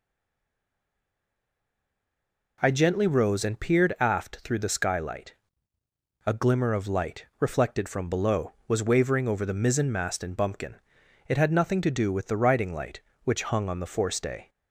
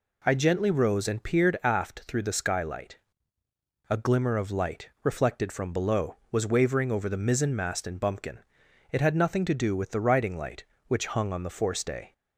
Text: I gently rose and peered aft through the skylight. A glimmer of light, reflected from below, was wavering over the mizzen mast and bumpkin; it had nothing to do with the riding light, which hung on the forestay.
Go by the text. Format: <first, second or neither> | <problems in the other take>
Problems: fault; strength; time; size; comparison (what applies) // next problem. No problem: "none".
second | stays silent before the first word; strong; until 2.5 s; 2.5 s long